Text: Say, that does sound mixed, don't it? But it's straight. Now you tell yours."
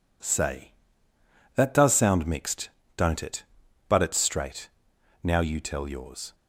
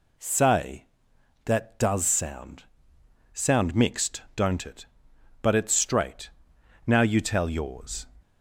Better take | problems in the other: first | says "sound" twice; at 3.3 s

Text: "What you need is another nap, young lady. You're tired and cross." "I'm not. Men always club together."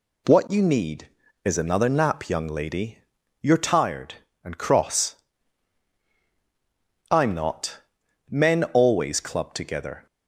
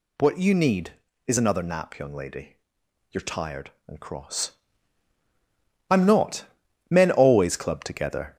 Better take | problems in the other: first | gets louder; slight; throughout; 3 dB

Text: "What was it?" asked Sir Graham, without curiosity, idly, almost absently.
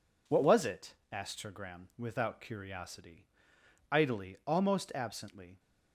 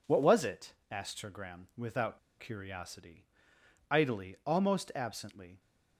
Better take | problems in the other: first | pauses between "without" and "curiosity"; slight; at 2.1 s; 0.20 s long

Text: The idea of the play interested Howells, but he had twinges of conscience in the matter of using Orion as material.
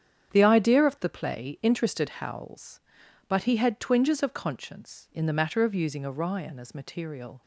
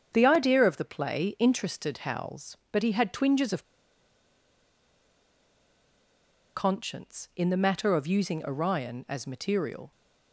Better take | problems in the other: first | starts louder than the rest; strong; until 1.1 s; 7.5 dB; strong in the first // pauses between "of" and "conscience"; strong; at 3.6 s; 2.9 s long

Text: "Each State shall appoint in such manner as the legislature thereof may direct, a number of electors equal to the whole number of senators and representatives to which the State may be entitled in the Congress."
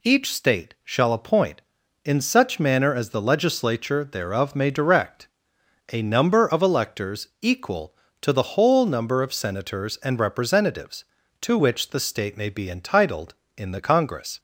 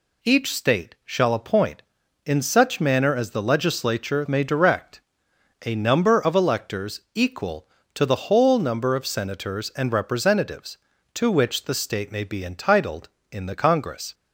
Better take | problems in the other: first | skips "thereof"; at 4.2 s // pauses between "electors" and "equal"; slight; at 6.9 s; 0.16 s long; slight in the first

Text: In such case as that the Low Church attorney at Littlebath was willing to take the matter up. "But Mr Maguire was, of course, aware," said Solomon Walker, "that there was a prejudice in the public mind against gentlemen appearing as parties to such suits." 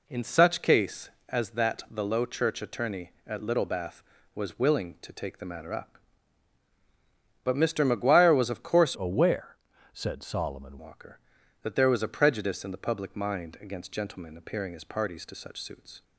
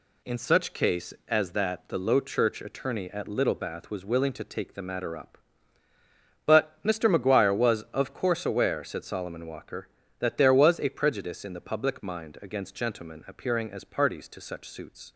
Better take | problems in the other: second | changes voice from "aware" to "Solomon"; from 8.9 to 10.7 s; 1.8 s long

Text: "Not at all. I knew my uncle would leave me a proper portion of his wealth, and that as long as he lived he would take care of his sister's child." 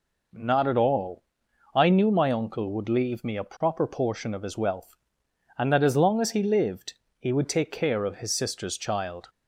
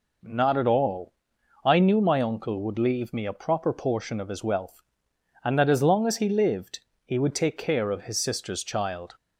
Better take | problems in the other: neither | pauses between "lived" and "he"; slight; the same in both

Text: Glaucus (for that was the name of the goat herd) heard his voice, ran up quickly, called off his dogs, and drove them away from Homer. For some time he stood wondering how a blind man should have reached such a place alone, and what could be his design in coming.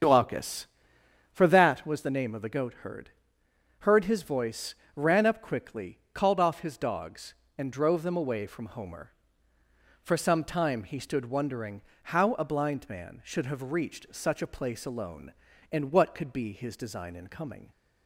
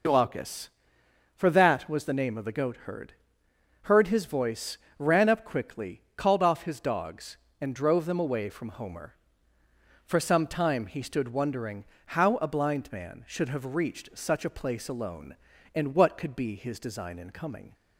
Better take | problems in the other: second | starts louder than the rest; strong; until 1.8 s; 7.5 dB // pauses between "wondering" and "how"; slight; at 11.8 s; 0.30 s long; slight in the second

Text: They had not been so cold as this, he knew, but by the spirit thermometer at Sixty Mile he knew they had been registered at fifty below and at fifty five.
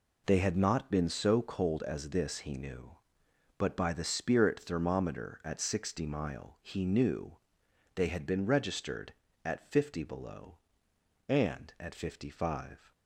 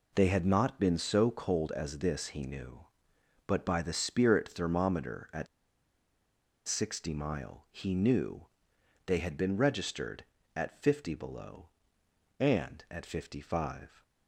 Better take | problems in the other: first | pauses between "at" and "Sixty"; at 5.4 s; 1.2 s long // pauses between "knew" and "they"; noticeable; at 8.4 s; 0.60 s long; noticeable in the first

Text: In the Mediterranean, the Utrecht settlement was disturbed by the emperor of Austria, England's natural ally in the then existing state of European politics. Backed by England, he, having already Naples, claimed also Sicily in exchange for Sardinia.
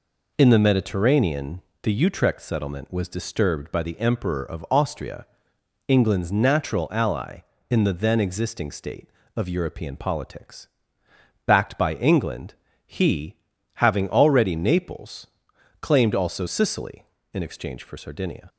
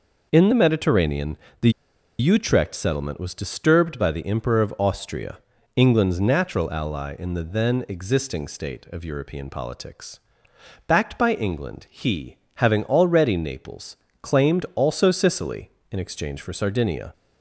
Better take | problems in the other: first | pauses between "the" and "Utrecht"; noticeable; at 1.6 s; 0.49 s long

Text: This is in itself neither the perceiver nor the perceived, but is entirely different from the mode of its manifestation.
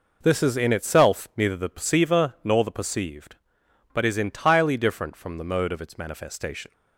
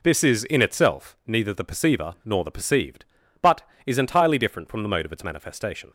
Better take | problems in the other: neither | none

